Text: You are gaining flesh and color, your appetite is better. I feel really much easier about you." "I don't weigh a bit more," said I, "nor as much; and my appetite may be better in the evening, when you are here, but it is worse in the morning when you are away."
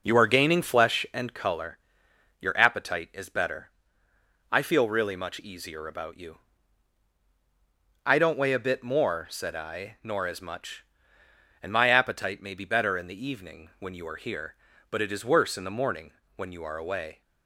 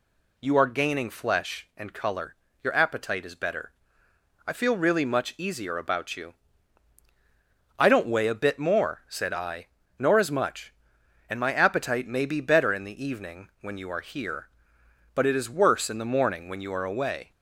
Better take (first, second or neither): second